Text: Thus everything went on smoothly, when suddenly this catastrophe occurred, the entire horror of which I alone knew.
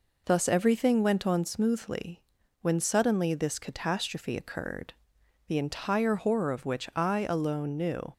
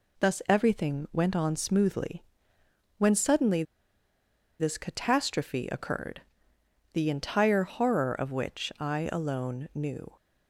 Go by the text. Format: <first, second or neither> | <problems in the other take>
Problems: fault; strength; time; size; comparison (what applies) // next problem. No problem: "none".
first | pauses between "suddenly" and "this"; noticeable; at 3.6 s; 0.97 s long